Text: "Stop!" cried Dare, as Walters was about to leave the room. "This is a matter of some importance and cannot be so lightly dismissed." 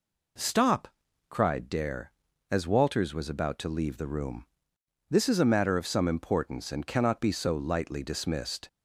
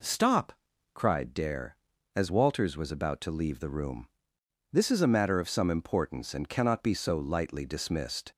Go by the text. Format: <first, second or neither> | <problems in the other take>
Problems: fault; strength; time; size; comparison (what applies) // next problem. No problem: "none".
neither | none